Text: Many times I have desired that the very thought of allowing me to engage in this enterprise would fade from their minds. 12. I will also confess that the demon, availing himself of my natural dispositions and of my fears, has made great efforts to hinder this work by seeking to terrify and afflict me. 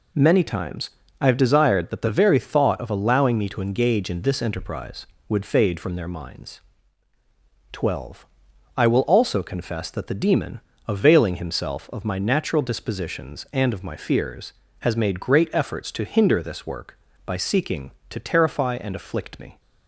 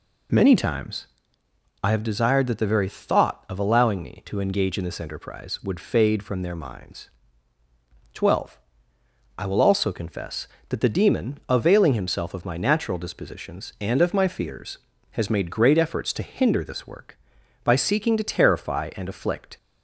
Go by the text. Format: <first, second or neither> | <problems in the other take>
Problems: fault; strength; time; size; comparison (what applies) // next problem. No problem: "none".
first | pauses between "times" and "I"; noticeable; at 1.0 s; 0.76 s long; slight in the first // stops before "me"; at 19.5 s